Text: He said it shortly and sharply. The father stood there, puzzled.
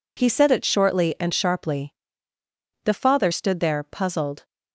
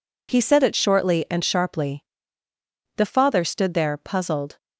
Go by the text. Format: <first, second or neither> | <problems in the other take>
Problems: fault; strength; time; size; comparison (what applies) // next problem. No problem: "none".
neither | none